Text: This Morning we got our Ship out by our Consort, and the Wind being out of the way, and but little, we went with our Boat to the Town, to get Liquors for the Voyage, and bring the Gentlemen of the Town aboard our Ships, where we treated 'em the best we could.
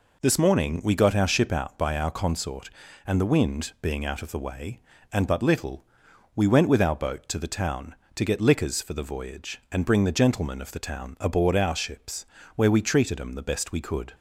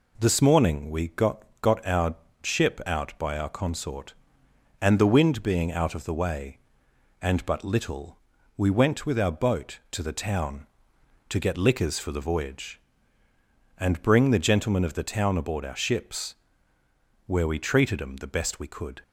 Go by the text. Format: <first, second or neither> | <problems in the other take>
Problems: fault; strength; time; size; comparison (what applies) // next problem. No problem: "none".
first | says "got" twice; at 1.6 s // pauses between "our" and "Ship"; slight; at 2.1 s; 0.28 s long